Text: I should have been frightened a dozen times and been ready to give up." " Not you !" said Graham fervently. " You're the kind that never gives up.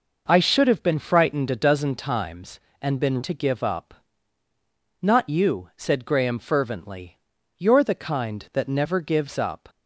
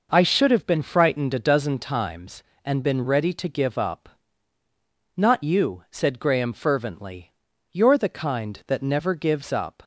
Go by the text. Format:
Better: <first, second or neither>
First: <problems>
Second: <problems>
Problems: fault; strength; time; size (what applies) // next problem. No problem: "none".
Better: second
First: skips "ready"; at 3.2 s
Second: none